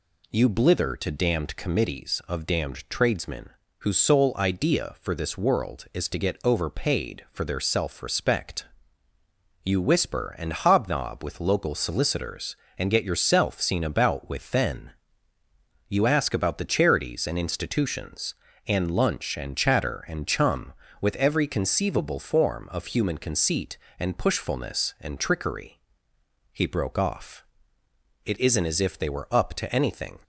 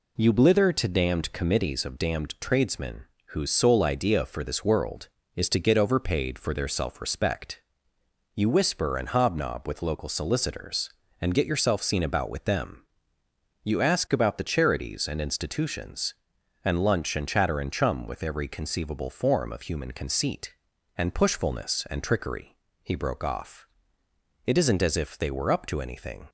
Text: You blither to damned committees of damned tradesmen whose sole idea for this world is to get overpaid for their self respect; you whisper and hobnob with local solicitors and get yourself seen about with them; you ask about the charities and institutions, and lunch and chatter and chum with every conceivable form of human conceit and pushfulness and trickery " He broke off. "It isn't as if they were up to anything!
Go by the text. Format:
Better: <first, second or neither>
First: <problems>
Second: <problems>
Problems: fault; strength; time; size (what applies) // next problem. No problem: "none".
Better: second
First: pauses between "tradesmen" and "whose"; slight; at 3.5 s; 0.28 s long // says "then" for "them"; at 14.5 s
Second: pauses between "tradesmen" and "whose"; slight; at 3.0 s; 0.24 s long